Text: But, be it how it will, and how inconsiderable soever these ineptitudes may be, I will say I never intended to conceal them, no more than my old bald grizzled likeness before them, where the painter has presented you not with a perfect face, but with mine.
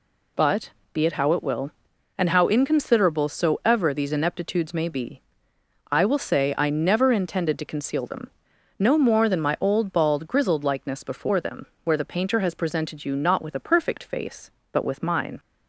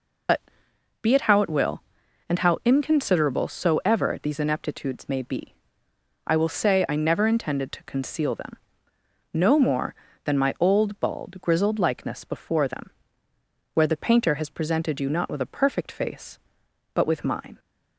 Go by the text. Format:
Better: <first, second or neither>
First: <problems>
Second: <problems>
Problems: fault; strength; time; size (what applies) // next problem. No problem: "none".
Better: first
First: none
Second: loses the start of "But"; at 0.2 s; 105 ms